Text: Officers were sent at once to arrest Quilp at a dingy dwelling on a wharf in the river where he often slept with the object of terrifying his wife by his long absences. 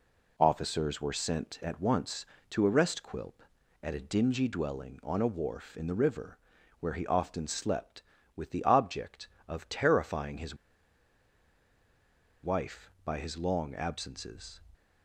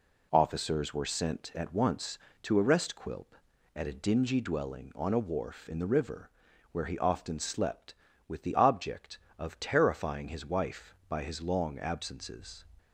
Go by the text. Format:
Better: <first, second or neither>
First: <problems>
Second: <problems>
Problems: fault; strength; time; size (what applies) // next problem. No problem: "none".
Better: second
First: pauses between "river" and "where"; at 6.3 s; 0.44 s long // pauses between "his" and "wife"; strong; at 10.5 s; 1.8 s long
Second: pauses between "river" and "where"; at 6.2 s; 0.44 s long